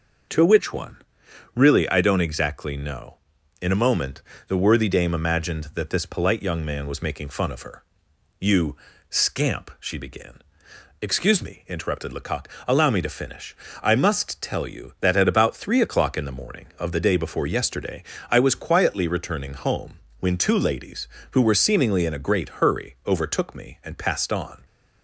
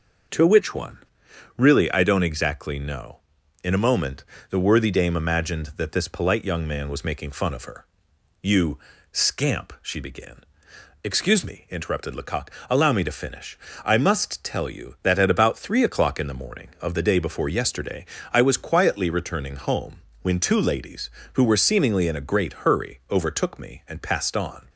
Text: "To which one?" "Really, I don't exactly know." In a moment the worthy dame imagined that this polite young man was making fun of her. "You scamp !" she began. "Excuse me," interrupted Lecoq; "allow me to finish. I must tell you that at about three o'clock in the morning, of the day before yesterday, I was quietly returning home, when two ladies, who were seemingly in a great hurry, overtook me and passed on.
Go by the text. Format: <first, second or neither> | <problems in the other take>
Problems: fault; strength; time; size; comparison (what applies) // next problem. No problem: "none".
neither | pauses between "moment" and "the"; slight; the same in both // pauses between "You" and "scamp"; slight; the same in both